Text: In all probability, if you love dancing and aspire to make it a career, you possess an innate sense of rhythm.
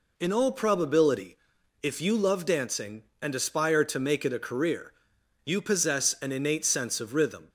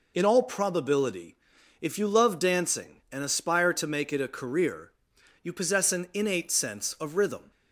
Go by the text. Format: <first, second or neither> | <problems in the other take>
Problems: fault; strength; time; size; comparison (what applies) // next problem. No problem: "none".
first | loses the start of "In"; at 0.1 s; 35 ms